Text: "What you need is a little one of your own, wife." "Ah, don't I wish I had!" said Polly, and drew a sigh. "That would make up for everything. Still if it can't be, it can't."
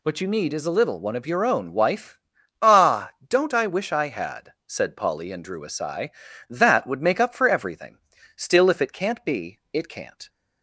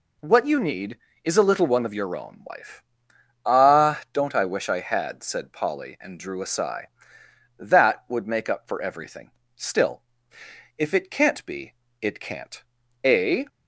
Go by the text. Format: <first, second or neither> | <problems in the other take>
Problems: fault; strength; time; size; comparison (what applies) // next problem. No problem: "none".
first | pauses between "Still" and "if"; noticeable; at 10.0 s; 0.74 s long // goes on to say "A"; slight; from 13.0 s on; 0.42 s long